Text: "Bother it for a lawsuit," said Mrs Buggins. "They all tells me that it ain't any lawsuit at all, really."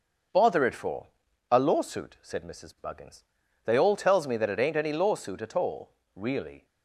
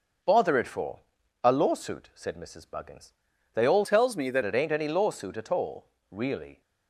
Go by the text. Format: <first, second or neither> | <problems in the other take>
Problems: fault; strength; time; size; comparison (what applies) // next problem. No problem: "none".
first | starts louder than the rest; until 1.6 s; 6.5 dB; also in the first // pauses between "for" and "a"; at 0.9 s; 0.42 s long; also in the first // changes voice from "tells" to "that"; from 3.8 to 4.4 s; 0.6 s long